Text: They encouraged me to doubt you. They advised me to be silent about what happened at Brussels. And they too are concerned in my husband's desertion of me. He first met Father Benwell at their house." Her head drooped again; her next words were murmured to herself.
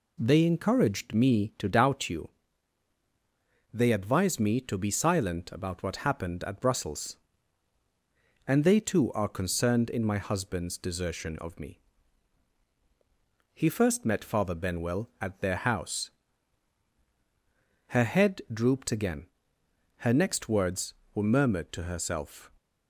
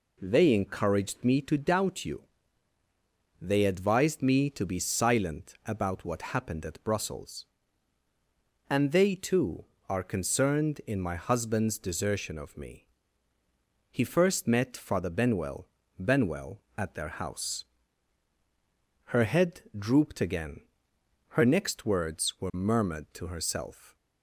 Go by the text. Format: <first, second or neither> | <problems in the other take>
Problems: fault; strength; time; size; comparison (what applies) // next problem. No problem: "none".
first | says "Benwell" twice; at 15.9 s